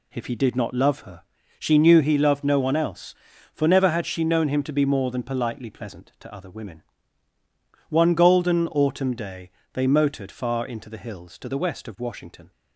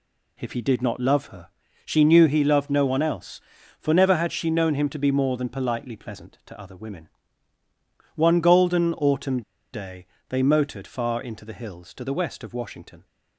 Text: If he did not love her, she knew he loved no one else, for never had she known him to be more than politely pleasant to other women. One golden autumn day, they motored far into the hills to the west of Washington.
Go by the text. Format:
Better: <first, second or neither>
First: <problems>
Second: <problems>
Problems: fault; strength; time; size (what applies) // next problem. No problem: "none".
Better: first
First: none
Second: pauses between "autumn" and "day"; slight; at 9.4 s; 0.32 s long